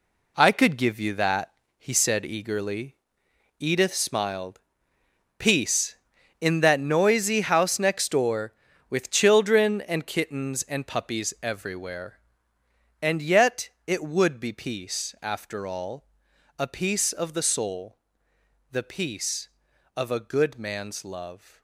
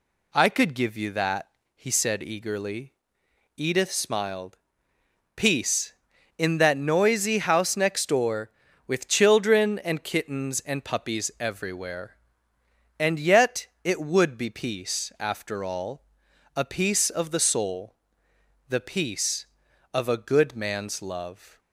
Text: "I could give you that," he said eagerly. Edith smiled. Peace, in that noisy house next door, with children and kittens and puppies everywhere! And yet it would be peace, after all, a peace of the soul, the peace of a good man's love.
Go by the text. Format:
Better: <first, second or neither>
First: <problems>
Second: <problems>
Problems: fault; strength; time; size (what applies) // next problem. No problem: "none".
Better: second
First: gets quieter; strong; throughout; 9.5 dB // pauses between "yet" and "it"; slight; at 13.6 s; 0.16 s long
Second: pauses between "yet" and "it"; slight; at 13.6 s; 0.16 s long